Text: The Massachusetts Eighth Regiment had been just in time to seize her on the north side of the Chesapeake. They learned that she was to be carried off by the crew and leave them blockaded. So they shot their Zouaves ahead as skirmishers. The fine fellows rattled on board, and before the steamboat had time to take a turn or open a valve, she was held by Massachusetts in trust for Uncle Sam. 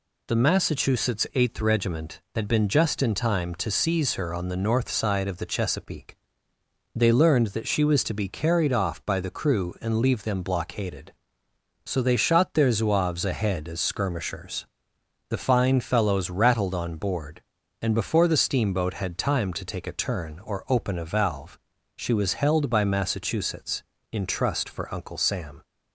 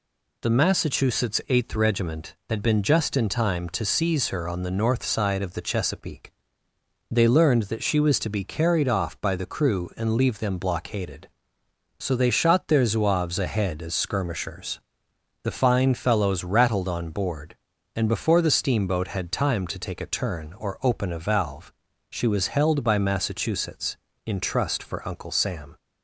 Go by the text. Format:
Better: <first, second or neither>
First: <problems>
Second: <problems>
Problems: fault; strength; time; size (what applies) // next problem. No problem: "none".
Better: neither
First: none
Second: none